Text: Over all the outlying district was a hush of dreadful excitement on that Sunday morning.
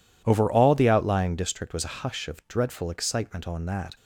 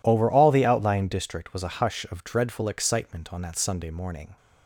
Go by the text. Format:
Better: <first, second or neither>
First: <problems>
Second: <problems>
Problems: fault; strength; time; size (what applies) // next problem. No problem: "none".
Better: second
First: stops before "Sunday morning"; at 3.9 s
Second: none